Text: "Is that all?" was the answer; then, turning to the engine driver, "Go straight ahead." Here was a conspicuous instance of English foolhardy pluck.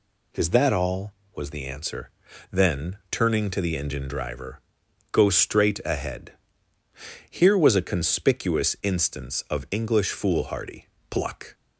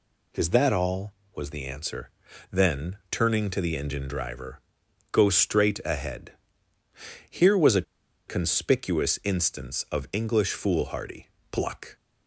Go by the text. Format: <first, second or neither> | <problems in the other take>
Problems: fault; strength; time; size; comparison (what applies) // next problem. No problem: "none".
first | pauses between "a" and "conspicuous"; at 7.8 s; 0.45 s long // pauses between "foolhardy" and "pluck"; slight; at 11.2 s; 0.24 s long; slight in the first